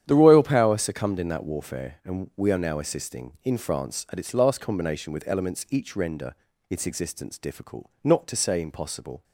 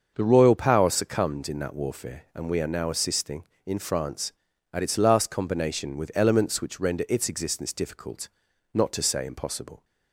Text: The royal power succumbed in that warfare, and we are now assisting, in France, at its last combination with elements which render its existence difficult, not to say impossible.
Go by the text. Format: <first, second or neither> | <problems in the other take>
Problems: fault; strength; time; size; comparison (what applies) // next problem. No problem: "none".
second | starts louder than the rest; strong; until 1.0 s; 9.5 dB; also in the second // says "each" for "which"; at 5.7 s // pauses between "render" and "its"; slight; at 6.3 s; 0.34 s long